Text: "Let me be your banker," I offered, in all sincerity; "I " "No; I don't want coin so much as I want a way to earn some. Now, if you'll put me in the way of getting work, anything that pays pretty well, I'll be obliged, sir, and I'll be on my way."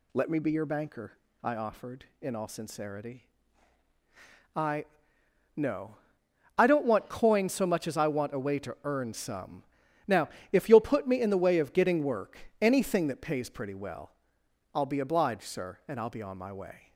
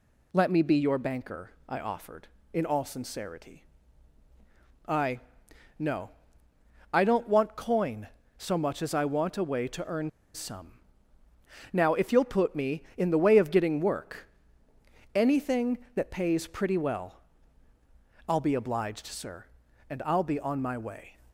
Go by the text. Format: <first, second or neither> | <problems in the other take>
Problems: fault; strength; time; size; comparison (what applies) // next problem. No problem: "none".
first | pauses between "earn" and "some"; slight; at 10.0 s; 0.24 s long